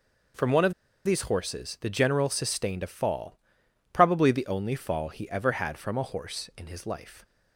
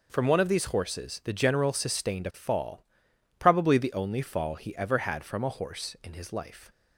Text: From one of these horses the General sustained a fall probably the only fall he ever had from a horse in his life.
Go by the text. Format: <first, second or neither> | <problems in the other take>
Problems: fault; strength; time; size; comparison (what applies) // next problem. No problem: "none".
second | pauses between "of" and "these"; slight; at 0.7 s; 0.32 s long // pauses between "fall" and "probably"; noticeable; at 3.3 s; 0.54 s long; noticeable in the second